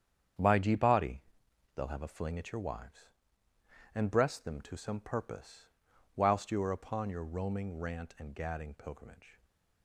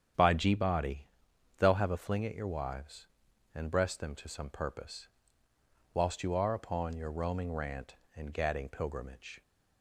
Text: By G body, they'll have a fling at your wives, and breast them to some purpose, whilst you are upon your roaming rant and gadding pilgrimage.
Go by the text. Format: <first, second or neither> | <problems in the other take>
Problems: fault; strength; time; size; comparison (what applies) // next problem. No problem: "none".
second | gets quieter; strong; throughout; 9 dB // starts louder than the rest; strong; until 1.9 s; 8.5 dB; strong in the second